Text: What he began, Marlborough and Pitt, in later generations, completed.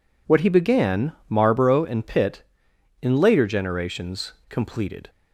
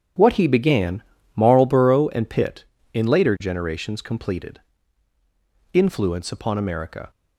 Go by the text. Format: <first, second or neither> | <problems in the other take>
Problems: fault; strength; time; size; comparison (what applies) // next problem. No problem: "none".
first | starts louder than the rest; strong; until 1.4 s; 8.5 dB // goes on to say "Influence Upon America"; from 5.7 s on; 1.3 s long